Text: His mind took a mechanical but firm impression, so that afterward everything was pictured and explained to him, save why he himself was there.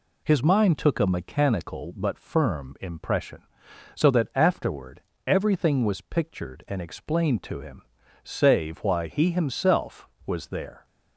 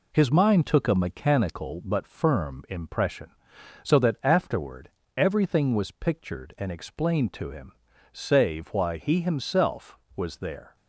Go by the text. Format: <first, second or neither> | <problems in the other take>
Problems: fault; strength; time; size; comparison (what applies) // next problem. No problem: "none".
first | gets quieter; noticeable; throughout; 4.5 dB // pauses between "afterward" and "everything"; slight; at 4.9 s; 0.26 s long; slight in the first